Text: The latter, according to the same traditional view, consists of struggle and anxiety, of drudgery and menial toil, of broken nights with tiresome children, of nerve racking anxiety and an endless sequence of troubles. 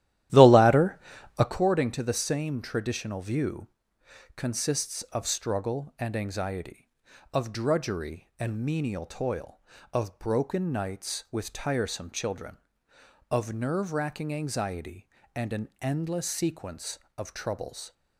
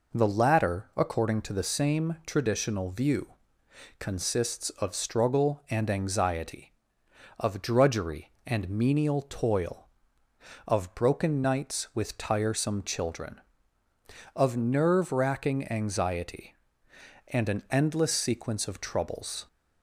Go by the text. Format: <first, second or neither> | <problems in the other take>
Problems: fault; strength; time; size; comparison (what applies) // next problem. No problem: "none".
second | starts louder than the rest; strong; until 1.6 s; 13 dB